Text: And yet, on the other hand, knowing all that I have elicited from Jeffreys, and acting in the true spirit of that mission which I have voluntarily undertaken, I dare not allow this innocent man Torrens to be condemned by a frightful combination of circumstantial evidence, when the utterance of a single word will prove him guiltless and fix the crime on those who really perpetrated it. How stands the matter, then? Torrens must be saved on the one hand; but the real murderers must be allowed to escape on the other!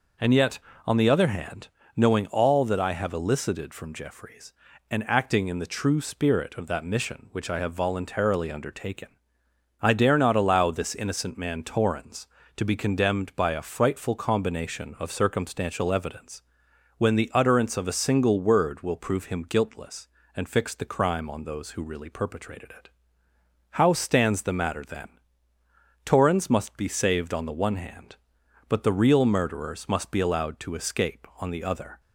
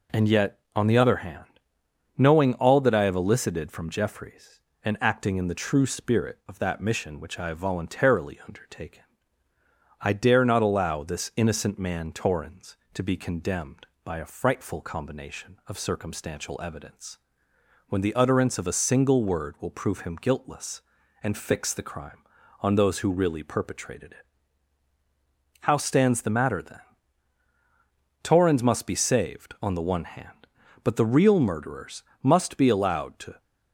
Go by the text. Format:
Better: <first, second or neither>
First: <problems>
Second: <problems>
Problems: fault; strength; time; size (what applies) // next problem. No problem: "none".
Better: first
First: none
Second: pauses between "murderers" and "must"; slight; at 32.0 s; 0.20 s long // stops before "escape on the other"; at 33.4 s